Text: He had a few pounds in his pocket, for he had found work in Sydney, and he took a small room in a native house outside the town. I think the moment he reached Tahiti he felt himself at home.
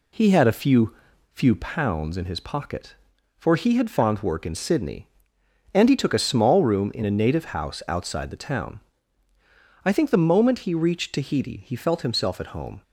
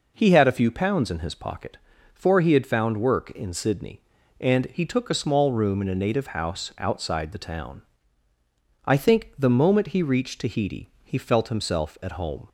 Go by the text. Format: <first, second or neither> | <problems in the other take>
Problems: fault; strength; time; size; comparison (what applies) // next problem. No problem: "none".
second | says "few" twice; at 1.3 s